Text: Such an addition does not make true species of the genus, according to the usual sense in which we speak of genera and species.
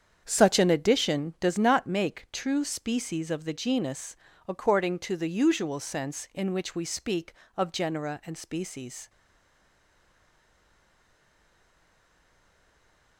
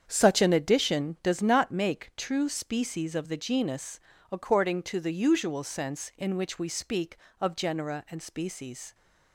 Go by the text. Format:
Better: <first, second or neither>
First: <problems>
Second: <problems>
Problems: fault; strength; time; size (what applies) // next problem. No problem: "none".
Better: second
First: starts louder than the rest; strong; until 1.2 s; 8 dB // stays silent after the last word; strong; from 9.0 s on; 4.1 s long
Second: starts louder than the rest; strong; until 1.1 s; 8 dB